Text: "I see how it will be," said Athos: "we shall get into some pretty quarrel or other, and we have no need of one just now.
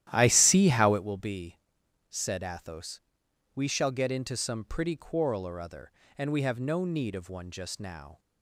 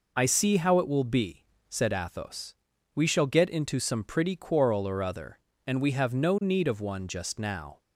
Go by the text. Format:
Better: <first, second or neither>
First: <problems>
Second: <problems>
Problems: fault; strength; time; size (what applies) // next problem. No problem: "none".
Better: second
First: starts louder than the rest; strong; until 1.1 s; 12.5 dB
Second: none